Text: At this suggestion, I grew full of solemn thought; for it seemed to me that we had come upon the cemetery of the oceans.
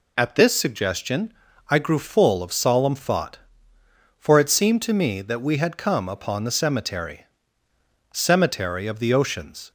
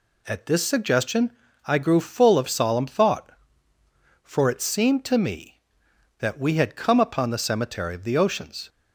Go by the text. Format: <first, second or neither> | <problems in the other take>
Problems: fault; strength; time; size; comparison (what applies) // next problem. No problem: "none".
second | says "cemetery" twice; at 8.1 s